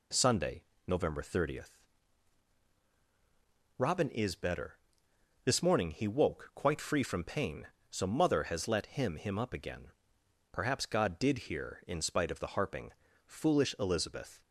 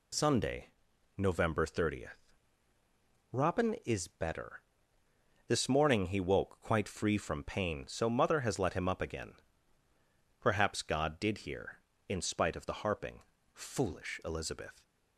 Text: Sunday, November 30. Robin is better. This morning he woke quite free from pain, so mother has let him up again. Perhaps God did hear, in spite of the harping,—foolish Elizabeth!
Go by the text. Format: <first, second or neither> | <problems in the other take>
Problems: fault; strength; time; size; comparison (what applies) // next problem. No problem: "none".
second | says "him" twice; at 9.1 s